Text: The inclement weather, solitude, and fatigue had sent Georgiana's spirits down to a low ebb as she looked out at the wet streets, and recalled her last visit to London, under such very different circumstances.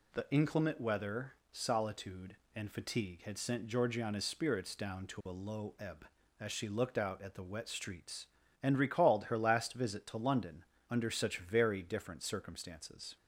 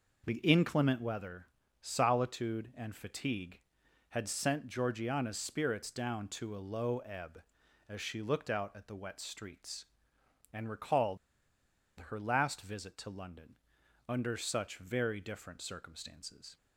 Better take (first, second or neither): first